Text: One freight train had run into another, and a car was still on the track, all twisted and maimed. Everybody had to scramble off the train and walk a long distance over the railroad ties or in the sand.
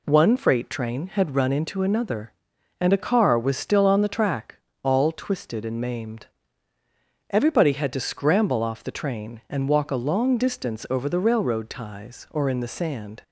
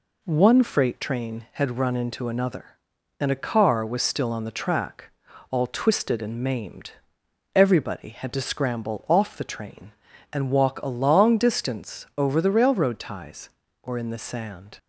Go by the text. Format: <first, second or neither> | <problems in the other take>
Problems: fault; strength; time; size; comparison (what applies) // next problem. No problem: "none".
neither | none